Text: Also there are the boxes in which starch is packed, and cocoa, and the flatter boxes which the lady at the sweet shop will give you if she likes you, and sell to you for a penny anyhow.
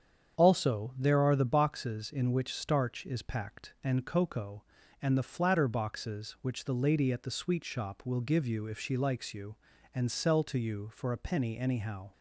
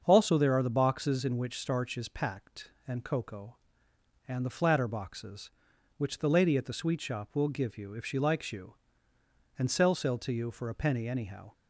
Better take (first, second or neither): first